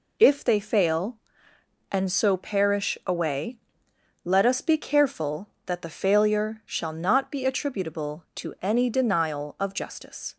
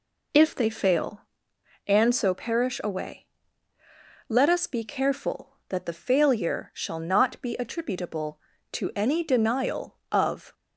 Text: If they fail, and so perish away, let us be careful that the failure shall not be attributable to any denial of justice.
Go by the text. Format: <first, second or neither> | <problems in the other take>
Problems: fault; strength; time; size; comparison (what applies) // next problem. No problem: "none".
first | stops before "justice"; at 10.5 s